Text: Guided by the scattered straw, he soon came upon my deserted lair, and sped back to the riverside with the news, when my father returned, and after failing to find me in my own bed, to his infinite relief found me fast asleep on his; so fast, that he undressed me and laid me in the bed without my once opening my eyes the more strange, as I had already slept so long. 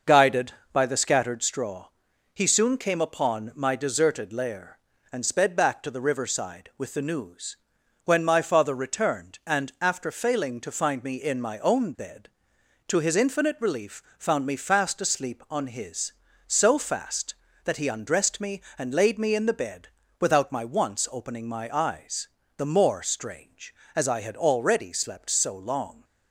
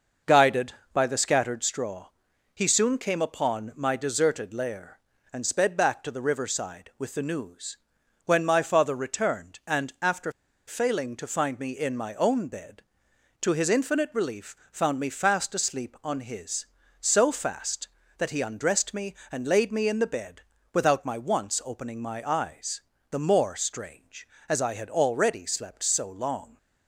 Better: first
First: pauses between "relief" and "found"; slight; at 13.9 s; 0.16 s long // pauses between "bed" and "without"; slight; at 19.8 s; 0.32 s long // pauses between "eyes" and "the"; slight; at 22.2 s; 0.30 s long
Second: starts louder than the rest; noticeable; until 1.4 s; 6 dB // pauses between "after" and "failing"; slight; at 10.3 s; 0.35 s long // pauses between "relief" and "found"; slight; at 14.5 s; 0.16 s long // pauses between "bed" and "without"; slight; at 20.4 s; 0.32 s long // pauses between "eyes" and "the"; slight; at 22.8 s; 0.30 s long

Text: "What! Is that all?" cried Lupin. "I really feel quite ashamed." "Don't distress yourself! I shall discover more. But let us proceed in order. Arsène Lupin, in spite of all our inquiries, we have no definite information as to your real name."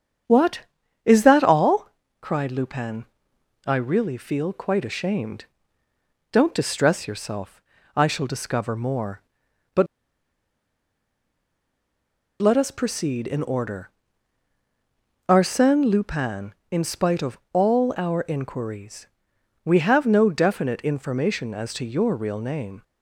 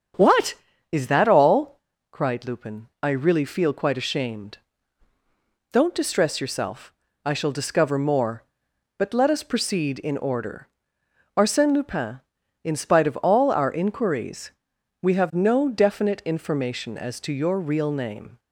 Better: second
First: starts louder than the rest; strong; until 1.7 s; 8 dB // pauses between "But" and "let"; strong; at 9.8 s; 2.5 s long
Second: starts louder than the rest; strong; until 1.5 s; 7.5 dB

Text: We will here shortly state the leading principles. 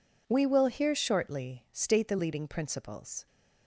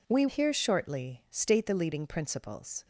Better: first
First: none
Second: skips "will"; at 0.2 s

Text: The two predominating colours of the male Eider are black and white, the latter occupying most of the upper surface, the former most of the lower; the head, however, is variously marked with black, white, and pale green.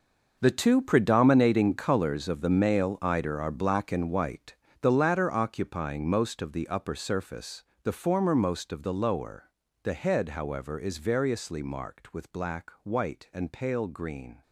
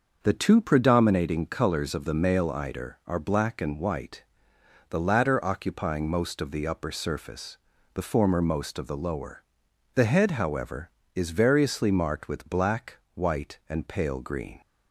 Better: second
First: gets quieter; strong; throughout; 14 dB // starts louder than the rest; noticeable; until 1.4 s; 6 dB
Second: starts louder than the rest; until 1.2 s; 6 dB

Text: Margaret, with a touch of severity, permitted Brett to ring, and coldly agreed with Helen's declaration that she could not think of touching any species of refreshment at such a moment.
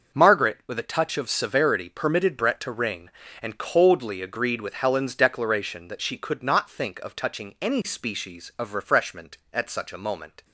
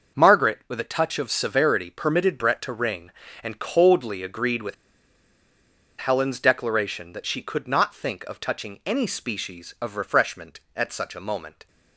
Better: first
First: starts louder than the rest; until 1.2 s; 6 dB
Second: starts louder than the rest; until 1.2 s; 6 dB // pauses between "with" and "Helen's"; at 4.7 s; 1.2 s long

